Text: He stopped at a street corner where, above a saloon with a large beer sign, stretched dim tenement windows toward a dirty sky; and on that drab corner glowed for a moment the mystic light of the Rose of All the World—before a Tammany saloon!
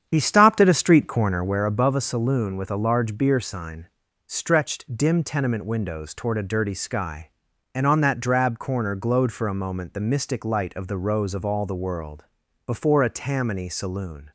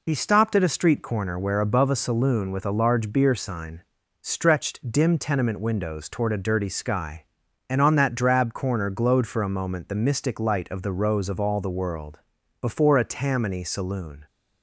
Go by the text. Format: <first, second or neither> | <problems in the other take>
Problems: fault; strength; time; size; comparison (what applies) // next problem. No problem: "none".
second | starts louder than the rest; strong; until 1.7 s; 8.5 dB